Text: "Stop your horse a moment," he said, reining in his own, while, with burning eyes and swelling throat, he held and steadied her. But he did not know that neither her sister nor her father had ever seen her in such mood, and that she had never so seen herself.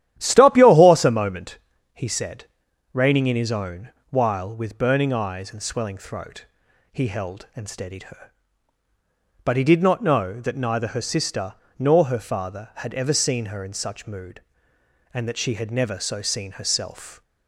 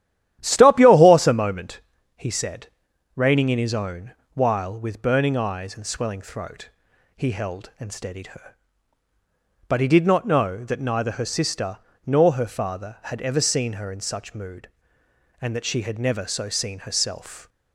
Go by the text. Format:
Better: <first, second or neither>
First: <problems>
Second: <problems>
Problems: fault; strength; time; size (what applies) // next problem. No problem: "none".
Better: neither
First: starts louder than the rest; strong; until 1.1 s; 12 dB // pauses between "sister" and "nor"; slight; at 11.5 s; 0.22 s long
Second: starts louder than the rest; strong; until 1.4 s; 12 dB // pauses between "sister" and "nor"; slight; at 11.7 s; 0.25 s long